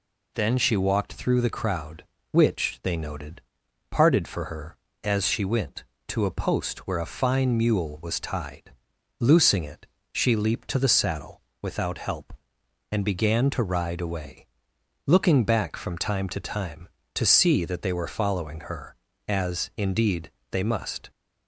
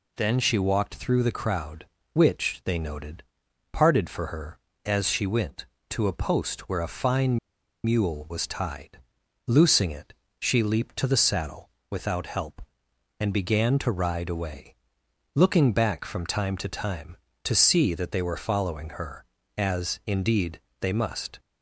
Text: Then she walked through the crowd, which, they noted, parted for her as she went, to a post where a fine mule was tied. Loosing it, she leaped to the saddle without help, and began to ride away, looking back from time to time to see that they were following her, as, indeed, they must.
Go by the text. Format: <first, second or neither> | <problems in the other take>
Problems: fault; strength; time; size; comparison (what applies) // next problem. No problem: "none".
first | pauses between "fine" and "mule"; noticeable; at 7.3 s; 0.46 s long // pauses between "saddle" and "without"; slight; at 11.6 s; 0.20 s long; slight in the first